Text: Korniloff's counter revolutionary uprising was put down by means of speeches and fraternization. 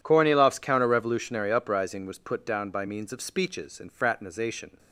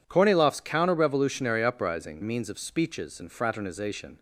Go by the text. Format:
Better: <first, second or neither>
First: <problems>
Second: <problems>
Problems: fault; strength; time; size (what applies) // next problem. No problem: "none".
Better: first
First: none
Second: skips "was put down by"; at 2.2 s